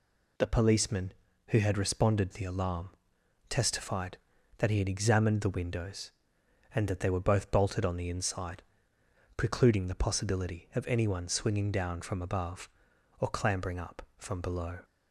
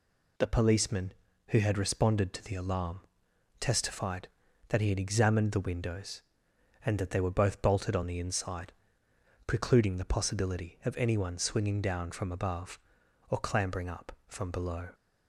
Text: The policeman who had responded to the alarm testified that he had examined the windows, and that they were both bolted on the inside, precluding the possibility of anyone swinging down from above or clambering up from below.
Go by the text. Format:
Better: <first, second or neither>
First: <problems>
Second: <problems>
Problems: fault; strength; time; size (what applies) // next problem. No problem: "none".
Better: second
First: skips "to"; at 2.3 s // pauses between "alarm" and "testified"; noticeable; at 2.8 s; 0.58 s long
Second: pauses between "alarm" and "testified"; noticeable; at 2.9 s; 0.58 s long